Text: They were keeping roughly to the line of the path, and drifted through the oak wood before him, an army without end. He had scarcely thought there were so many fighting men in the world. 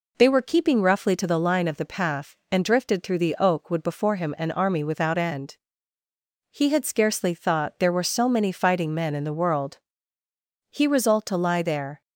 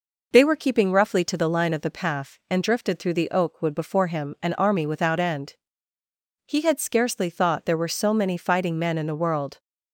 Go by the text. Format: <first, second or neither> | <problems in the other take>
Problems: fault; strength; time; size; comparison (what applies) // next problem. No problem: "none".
second | goes on to say "He resolved to lie there"; noticeable; from 10.7 s on; 1.3 s long